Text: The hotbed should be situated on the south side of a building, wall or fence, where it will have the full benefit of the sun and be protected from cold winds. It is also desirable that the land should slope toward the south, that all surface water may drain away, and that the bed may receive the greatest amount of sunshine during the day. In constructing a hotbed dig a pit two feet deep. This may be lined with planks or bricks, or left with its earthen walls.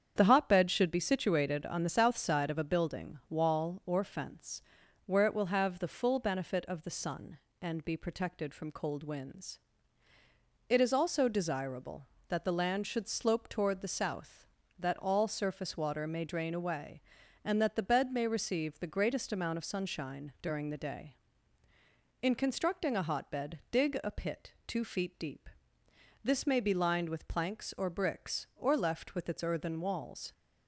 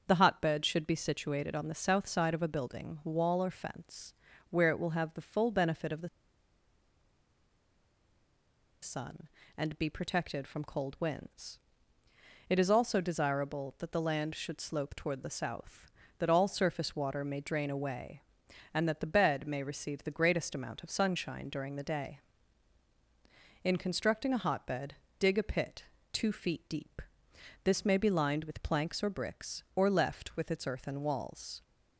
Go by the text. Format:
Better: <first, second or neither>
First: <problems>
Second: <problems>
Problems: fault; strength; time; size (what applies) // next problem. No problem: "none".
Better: first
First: starts louder than the rest; strong; until 1.1 s; 8 dB // pauses between "pit" and "two"; slight; at 24.5 s; 0.16 s long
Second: starts louder than the rest; until 1.0 s; 7 dB // pauses between "the" and "sun"; strong; at 6.0 s; 2.7 s long // pauses between "hotbed" and "dig"; slight; at 24.9 s; 0.24 s long // pauses between "pit" and "two"; slight; at 25.8 s; 0.28 s long